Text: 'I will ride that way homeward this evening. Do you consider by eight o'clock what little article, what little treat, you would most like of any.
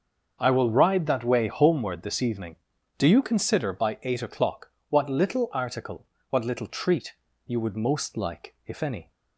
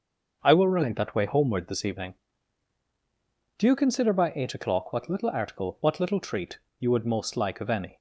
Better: second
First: starts louder than the rest; until 1.4 s; 6.5 dB // pauses between "o'clock" and "what"; slight; at 4.7 s; 0.18 s long // says "if" for "of"; at 8.6 s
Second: starts louder than the rest; until 1.4 s; 6 dB

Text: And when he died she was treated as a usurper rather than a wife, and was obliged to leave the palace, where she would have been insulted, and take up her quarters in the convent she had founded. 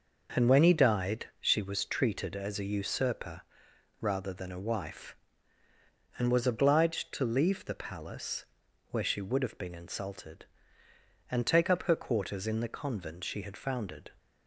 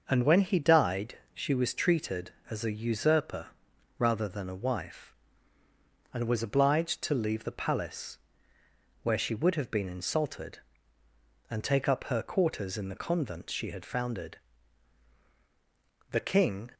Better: first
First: pauses between "usurper" and "rather"; noticeable; at 3.4 s; 0.58 s long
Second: starts louder than the rest; until 1.1 s; 6 dB // pauses between "died" and "she"; slight; at 1.1 s; 0.18 s long // pauses between "usurper" and "rather"; noticeable; at 3.4 s; 0.50 s long // goes on to say "The King"; from 16.1 s on; 0.60 s long

